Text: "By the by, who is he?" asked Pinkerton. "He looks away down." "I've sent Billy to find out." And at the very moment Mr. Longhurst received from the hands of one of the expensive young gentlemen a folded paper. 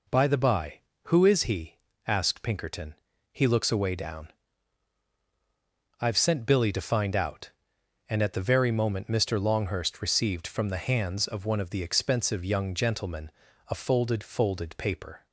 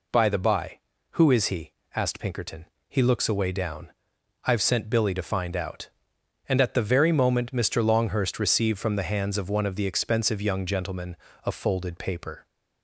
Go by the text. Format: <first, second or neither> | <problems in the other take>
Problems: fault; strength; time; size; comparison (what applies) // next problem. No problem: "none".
second | pauses between "gentlemen" and "a"; slight; at 13.3 s; 0.36 s long; slight in the second // says "folded" twice; at 14.2 s